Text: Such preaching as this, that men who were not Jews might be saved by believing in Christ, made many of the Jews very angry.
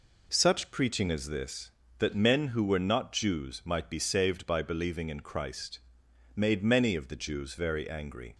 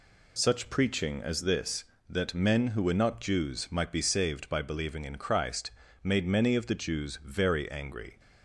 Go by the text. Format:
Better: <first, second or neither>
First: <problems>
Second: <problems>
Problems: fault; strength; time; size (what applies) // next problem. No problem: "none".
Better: neither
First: none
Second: none